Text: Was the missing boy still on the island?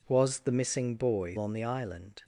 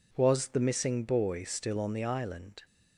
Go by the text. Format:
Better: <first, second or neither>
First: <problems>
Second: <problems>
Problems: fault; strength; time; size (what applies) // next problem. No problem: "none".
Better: second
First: skips "still"; at 1.3 s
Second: none